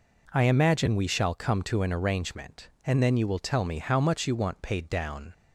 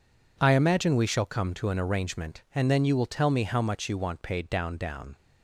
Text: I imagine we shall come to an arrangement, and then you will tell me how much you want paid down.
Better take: first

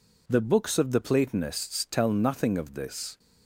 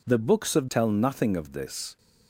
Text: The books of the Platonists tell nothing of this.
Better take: first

